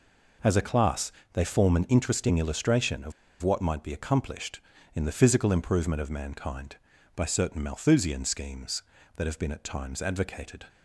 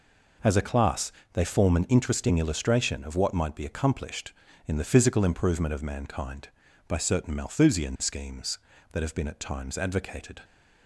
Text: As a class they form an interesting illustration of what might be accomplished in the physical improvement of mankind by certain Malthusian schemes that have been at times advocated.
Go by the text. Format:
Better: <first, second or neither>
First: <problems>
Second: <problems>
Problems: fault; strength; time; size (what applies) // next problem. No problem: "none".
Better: second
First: pauses between "class" and "they"; slight; at 1.1 s; 0.22 s long // pauses between "of" and "what"; slight; at 3.1 s; 0.29 s long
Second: pauses between "class" and "they"; slight; at 1.1 s; 0.22 s long